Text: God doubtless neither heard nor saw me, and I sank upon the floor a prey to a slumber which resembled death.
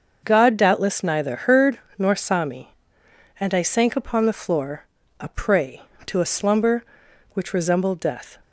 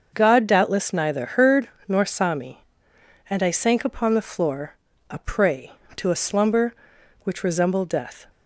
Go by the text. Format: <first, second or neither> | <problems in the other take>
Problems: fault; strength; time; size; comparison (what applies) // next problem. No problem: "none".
neither | starts louder than the rest; noticeable; the same in both // pauses between "heard" and "nor"; slight; the same in both // pauses between "floor" and "a"; slight; the same in both